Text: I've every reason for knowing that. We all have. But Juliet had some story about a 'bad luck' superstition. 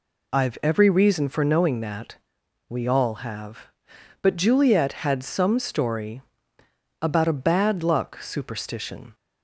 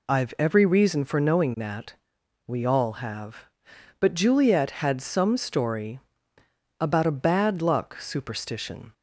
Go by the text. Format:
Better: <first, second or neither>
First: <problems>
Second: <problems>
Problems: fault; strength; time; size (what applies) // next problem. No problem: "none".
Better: neither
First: pauses between "story" and "about"; noticeable; at 6.2 s; 0.79 s long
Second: pauses between "story" and "about"; noticeable; at 5.9 s; 0.80 s long